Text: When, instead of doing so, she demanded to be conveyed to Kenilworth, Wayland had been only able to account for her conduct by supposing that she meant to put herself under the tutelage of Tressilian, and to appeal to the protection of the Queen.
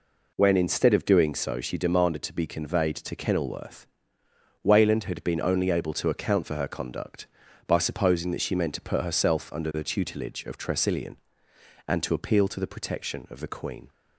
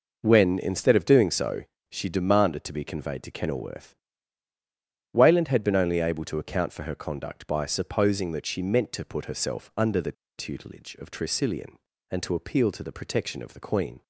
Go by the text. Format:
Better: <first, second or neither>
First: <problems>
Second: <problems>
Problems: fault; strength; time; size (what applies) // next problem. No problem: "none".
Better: first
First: none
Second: pauses between "the" and "tutelage"; slight; at 10.1 s; 0.25 s long